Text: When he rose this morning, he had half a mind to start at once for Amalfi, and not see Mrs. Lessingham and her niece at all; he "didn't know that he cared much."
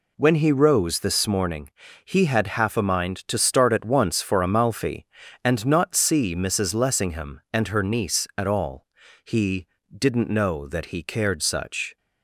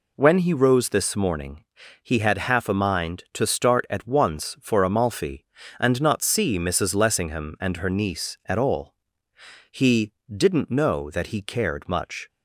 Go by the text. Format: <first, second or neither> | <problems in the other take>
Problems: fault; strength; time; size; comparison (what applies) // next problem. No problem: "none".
second | pauses between "he" and "didn't"; slight; at 9.6 s; 0.24 s long; slight in the second // says "such" for "much"; at 11.4 s